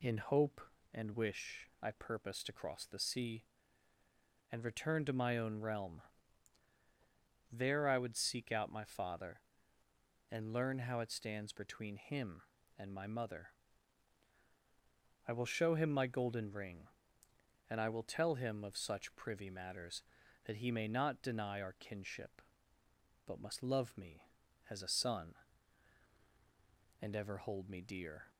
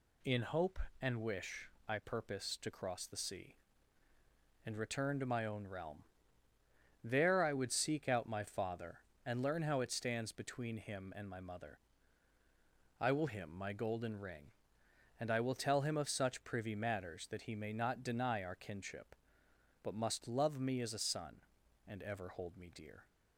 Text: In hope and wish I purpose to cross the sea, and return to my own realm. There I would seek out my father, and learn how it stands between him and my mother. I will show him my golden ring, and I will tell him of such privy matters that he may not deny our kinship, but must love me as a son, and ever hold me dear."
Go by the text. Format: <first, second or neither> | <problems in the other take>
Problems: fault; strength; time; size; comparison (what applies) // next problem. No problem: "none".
first | pauses between "wish" and "I"; slight; at 1.6 s; 0.18 s long // skips "show"; at 13.2 s